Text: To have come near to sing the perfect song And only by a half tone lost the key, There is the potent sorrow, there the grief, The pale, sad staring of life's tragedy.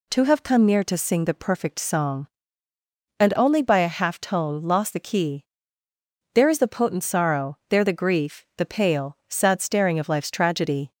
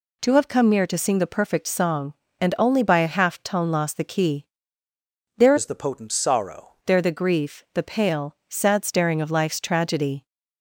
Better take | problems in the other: first | changes voice from "is" to "sorrow"; from 5.5 to 6.6 s; 1.1 s long

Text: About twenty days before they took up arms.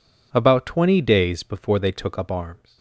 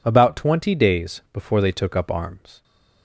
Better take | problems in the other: neither | none

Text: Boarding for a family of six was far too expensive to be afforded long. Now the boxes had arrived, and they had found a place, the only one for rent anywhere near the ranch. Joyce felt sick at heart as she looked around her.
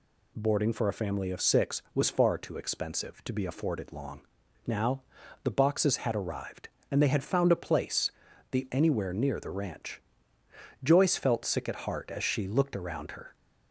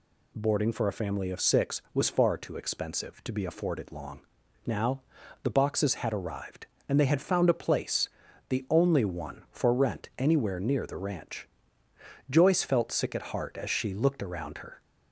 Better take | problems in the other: second | pauses between "Now" and "the"; at 5.0 s; 0.42 s long; also in the second // skips "only one for rent"; at 8.6 s

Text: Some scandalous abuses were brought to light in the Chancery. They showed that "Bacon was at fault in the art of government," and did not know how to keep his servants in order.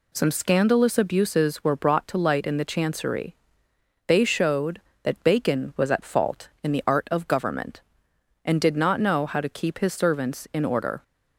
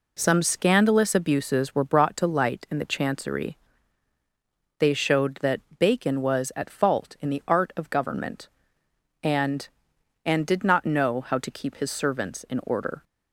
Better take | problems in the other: first | pauses between "that" and "Bacon"; slight; at 5.5 s; 0.18 s long // says "and" twice; at 10.2 s

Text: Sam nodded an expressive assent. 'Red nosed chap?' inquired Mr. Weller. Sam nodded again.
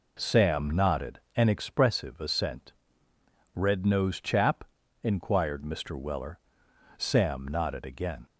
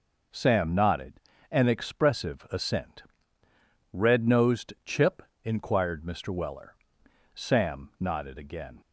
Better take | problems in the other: first | pauses between "nodded" and "an"; slight; at 1.1 s; 0.32 s long // says "chip" for "chap"; at 4.8 s

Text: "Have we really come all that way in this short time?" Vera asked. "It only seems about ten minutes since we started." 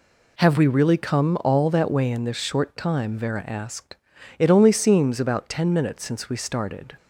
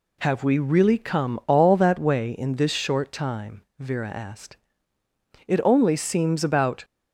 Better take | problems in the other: first | stops before "ten minutes since we started"; at 6.8 s

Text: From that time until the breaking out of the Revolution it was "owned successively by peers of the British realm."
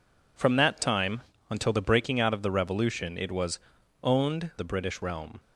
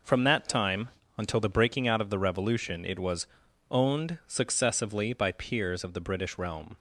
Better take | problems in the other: second | pauses between "time" and "until"; slight; at 1.2 s; 0.28 s long; slight in the second // pauses between "was" and "owned"; noticeable; at 3.5 s; 0.46 s long; noticeable in the second // skips "successively by peers of"; at 4.5 s

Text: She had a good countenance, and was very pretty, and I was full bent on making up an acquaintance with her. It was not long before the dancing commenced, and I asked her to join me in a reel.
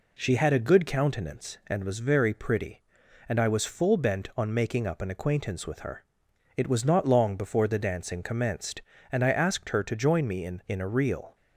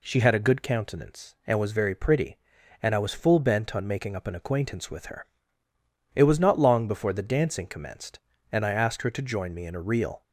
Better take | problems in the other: second | says "in" twice; at 10.6 s

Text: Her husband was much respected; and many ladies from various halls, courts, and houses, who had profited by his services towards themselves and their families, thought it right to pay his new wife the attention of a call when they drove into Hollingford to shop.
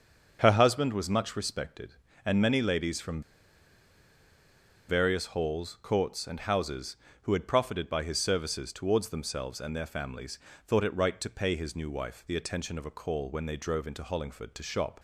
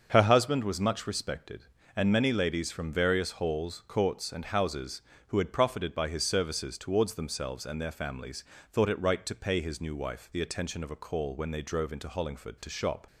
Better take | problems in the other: second | starts louder than the rest; until 1.4 s; 7 dB; also in the second // pauses between "from" and "various"; strong; at 3.2 s; 1.6 s long

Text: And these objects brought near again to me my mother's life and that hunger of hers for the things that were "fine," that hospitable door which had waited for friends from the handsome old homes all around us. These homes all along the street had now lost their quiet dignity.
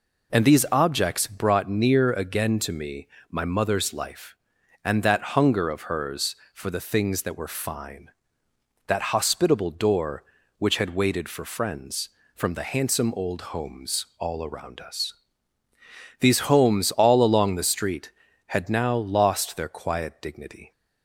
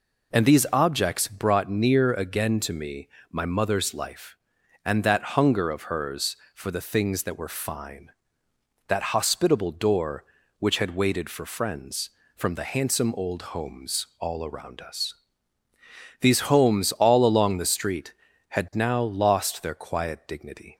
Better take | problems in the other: neither | pauses between "me" and "my"; slight; the same in both

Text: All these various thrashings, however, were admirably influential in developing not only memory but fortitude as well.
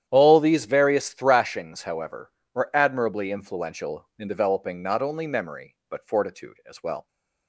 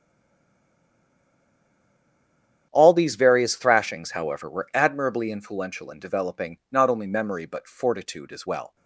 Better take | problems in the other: first | stays silent before the first word; strong; until 2.7 s; 2.7 s long // starts louder than the rest; strong; until 3.7 s; 9 dB; strong in the first

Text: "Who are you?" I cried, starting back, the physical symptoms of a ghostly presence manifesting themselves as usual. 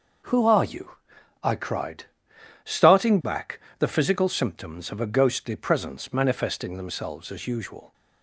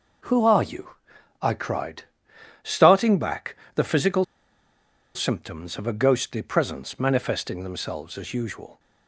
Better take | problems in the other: first | pauses between "physical" and "symptoms"; noticeable; at 4.2 s; 0.91 s long

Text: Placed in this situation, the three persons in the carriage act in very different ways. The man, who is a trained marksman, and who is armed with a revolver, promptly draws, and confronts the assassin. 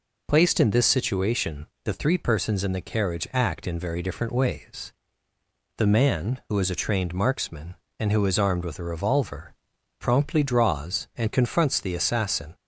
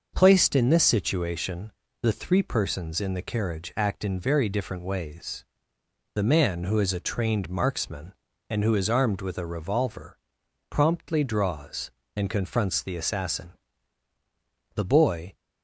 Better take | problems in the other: first | goes on to say "The boy"; from 14.7 s on; 0.58 s long

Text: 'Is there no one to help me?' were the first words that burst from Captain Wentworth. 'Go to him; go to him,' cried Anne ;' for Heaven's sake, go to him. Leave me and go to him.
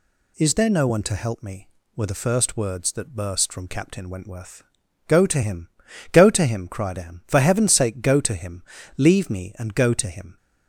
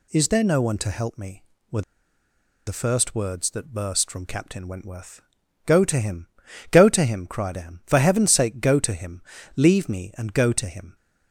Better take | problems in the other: first | pauses between "were" and "the"; noticeable; at 1.8 s; 0.84 s long

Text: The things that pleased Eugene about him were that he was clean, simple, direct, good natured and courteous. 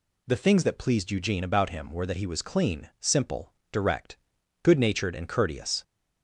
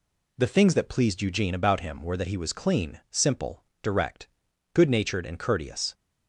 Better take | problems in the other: first | gets quieter; slight; throughout; 2.5 dB

